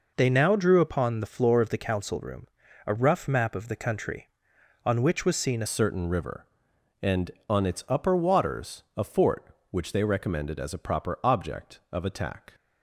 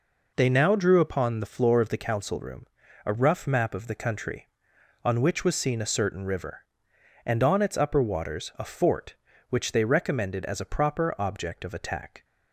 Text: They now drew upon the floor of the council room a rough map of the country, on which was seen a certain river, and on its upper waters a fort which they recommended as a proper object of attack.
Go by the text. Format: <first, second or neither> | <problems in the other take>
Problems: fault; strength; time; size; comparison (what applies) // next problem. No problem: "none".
second | pauses between "room" and "a"; at 2.4 s; 0.38 s long; also in the second // changes voice at "certain"; from 5.6 s on; 6.9 s long